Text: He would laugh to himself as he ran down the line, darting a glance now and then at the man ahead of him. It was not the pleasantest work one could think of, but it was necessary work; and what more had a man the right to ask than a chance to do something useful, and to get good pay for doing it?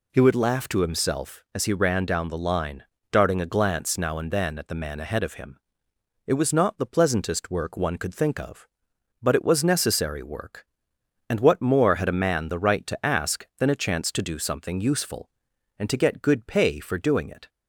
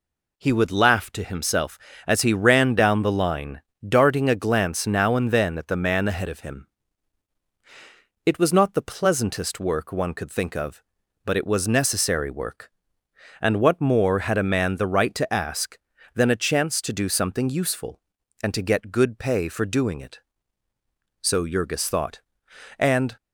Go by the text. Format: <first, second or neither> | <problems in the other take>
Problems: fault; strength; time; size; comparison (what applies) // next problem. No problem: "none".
first | goes on to say "So Jurgis thought and"; strong; from 21.2 s on; 1.9 s long